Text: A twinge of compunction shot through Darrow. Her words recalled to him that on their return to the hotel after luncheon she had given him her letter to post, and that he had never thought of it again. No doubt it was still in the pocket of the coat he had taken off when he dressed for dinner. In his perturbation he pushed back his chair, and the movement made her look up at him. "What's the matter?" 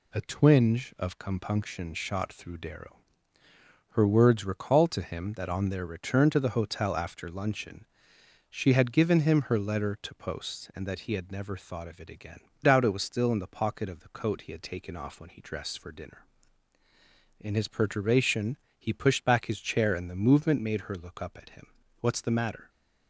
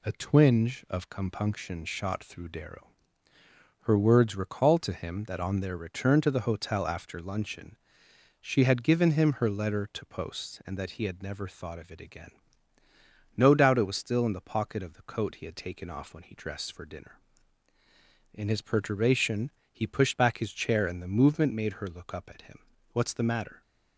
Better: second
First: pauses between "luncheon" and "she"; noticeable; at 7.8 s; 0.64 s long // skips "No"; at 12.5 s // pauses between "perturbation" and "he"; slight; at 18.5 s; 0.20 s long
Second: pauses between "luncheon" and "she"; noticeable; at 7.7 s; 0.64 s long // pauses between "perturbation" and "he"; slight; at 19.5 s; 0.20 s long

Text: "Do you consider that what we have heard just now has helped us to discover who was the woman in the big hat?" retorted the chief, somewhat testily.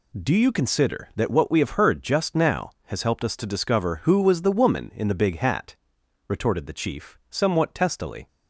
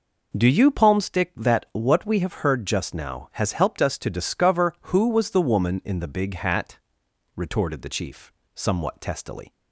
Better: first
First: none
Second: says "palmstick" for "consider"; at 0.7 s

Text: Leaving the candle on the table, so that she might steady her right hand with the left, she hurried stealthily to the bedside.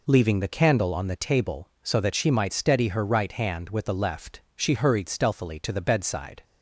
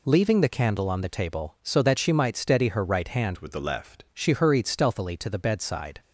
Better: first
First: none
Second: changes voice from "with" to "left"; from 3.3 to 4.0 s; 0.7 s long

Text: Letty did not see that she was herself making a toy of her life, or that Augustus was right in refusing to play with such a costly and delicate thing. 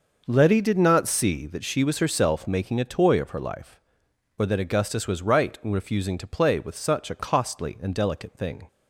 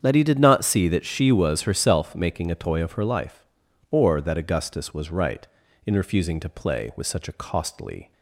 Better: first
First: none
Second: starts louder than the rest; strong; until 1.0 s; 8 dB // stops before "and delicate thing"; at 8.1 s

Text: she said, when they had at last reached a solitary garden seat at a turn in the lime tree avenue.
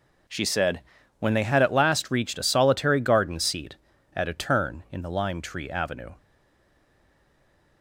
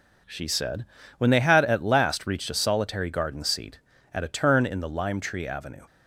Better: second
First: stays silent after the last word; noticeable; from 6.1 s on; 1.7 s long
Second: none

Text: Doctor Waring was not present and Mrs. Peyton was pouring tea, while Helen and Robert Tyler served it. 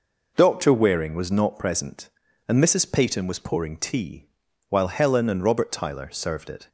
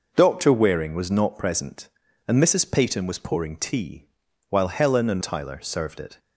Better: first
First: none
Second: skips "Robert"; at 5.2 s

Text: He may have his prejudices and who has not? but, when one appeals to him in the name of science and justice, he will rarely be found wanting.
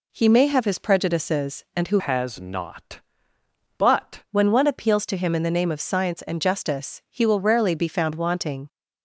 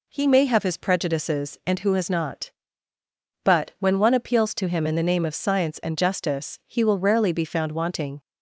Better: second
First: changes voice from "has" to "but"; from 1.9 to 4.2 s; 2.3 s long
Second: none

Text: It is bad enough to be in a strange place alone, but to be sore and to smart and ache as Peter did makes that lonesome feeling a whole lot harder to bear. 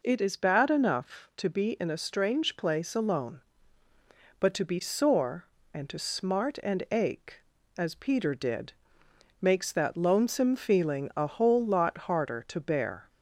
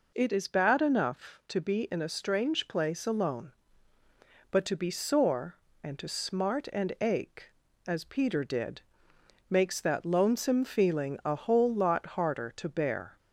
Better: neither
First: pauses between "did" and "makes"; noticeable; at 8.7 s; 0.68 s long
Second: pauses between "did" and "makes"; noticeable; at 8.8 s; 0.68 s long

